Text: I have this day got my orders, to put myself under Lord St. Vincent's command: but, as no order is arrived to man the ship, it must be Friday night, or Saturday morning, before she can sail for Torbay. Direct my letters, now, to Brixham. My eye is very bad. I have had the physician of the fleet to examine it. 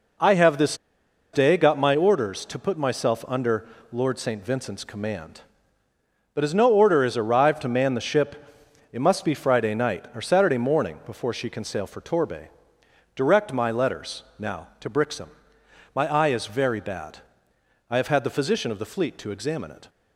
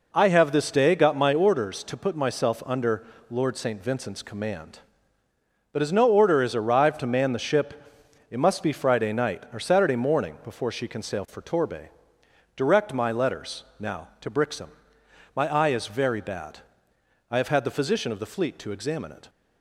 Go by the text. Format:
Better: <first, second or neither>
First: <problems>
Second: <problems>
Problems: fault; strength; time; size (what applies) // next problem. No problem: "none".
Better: second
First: pauses between "this" and "day"; noticeable; at 0.7 s; 0.56 s long // pauses between "under" and "Lord"; slight; at 3.6 s; 0.24 s long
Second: pauses between "under" and "Lord"; slight; at 3.0 s; 0.24 s long